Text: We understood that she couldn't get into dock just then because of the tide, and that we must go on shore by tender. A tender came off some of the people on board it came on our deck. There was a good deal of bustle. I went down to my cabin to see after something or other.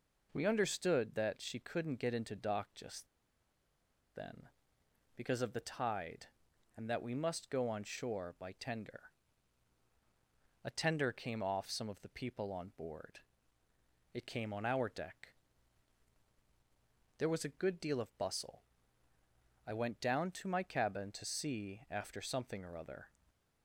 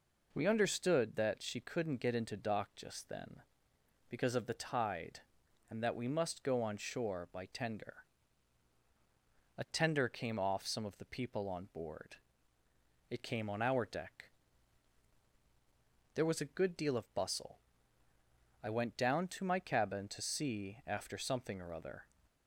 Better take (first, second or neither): second